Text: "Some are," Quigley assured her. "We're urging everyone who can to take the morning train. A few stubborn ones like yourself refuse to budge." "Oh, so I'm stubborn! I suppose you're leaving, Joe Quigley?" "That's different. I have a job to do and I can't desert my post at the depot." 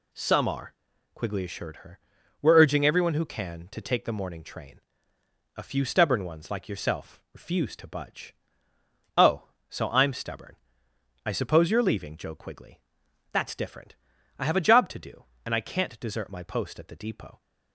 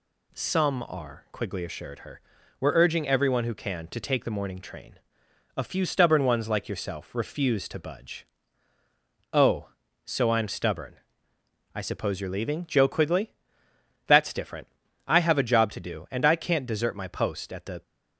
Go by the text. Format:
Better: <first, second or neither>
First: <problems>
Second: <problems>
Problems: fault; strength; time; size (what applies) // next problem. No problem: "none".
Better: first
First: none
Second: stops before "depot"; at 17.8 s